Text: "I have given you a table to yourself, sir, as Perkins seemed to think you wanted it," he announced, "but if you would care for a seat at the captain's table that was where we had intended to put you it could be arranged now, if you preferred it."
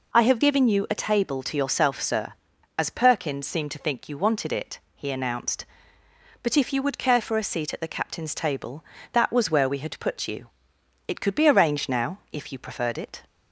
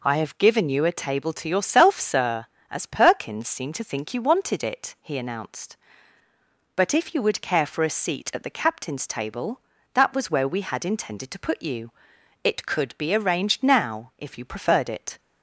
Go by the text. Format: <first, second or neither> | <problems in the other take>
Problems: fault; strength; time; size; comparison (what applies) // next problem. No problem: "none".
second | skips "intended to"; at 9.9 s // pauses between "you" and "it"; noticeable; at 10.4 s; 0.58 s long; noticeable in the second